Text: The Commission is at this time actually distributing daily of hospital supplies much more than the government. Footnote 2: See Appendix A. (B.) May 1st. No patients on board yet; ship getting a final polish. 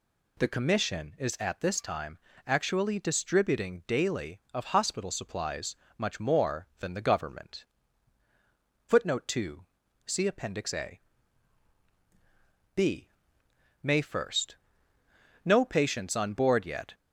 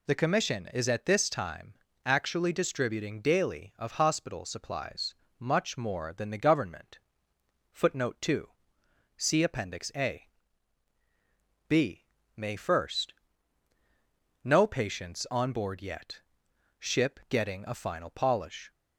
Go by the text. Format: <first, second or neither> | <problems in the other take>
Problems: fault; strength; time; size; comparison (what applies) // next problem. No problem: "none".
second | pauses between "time" and "actually"; slight; at 2.1 s; 0.28 s long; slight in the second // pauses between "supplies" and "much"; slight; at 5.7 s; 0.24 s long; slight in the second // stops before "ship getting a final polish"; at 16.9 s